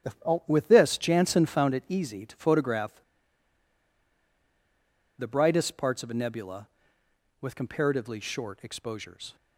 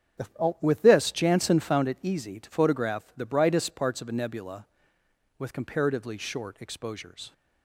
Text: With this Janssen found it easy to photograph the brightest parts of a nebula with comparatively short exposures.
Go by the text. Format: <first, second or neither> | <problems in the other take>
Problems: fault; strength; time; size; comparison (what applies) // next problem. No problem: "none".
second | starts louder than the rest; strong; until 1.4 s; 11 dB; strong in the second // pauses between "photograph" and "the"; strong; at 2.9 s; 2.1 s long